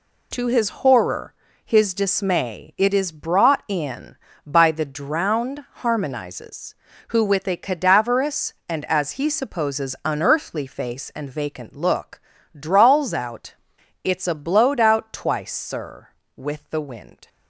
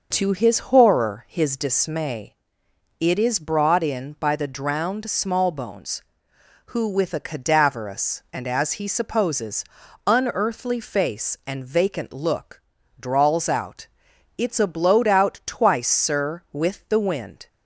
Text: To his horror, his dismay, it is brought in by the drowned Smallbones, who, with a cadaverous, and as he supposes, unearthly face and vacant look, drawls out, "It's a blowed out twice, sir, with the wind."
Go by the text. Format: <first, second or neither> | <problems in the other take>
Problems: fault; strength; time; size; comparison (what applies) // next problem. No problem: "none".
second | says "Harmonizes" for "Smallbones"; at 5.8 s